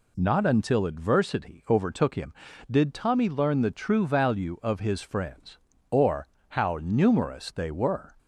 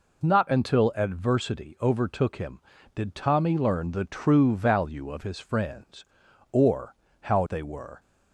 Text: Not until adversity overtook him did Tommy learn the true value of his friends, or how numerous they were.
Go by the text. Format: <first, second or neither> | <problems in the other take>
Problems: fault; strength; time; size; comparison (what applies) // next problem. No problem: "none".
first | pauses between "or" and "how"; slight; at 6.9 s; 0.28 s long; slight in the first // skips "numerous"; at 7.4 s